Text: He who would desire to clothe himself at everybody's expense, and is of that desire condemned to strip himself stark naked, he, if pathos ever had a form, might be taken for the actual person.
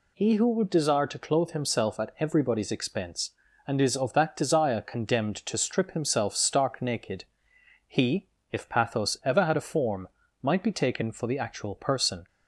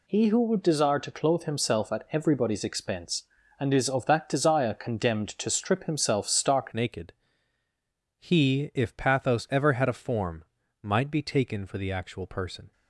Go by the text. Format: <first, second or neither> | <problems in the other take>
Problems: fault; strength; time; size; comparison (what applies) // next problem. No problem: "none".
first | changes voice at "naked"; from 6.7 s on; 6.0 s long